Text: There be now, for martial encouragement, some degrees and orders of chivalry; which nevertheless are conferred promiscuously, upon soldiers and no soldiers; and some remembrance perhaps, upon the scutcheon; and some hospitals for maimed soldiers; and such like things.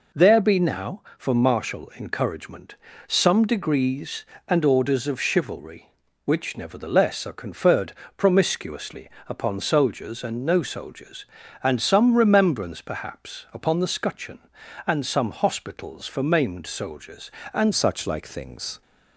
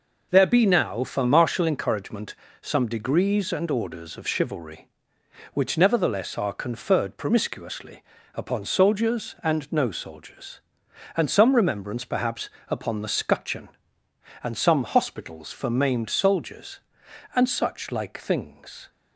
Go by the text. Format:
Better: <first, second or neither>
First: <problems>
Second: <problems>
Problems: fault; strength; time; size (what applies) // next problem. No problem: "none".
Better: second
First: pauses between "conferred" and "promiscuously"; slight; at 7.9 s; 0.24 s long // changes voice at "such"; from 17.7 s on; 1.1 s long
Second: none